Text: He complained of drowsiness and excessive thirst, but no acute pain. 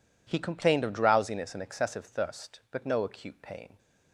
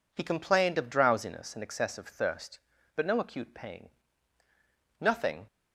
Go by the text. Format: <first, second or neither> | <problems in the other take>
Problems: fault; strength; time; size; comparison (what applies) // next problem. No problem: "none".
first | goes on to say "Nothing"; slight; from 5.0 s on; 0.46 s long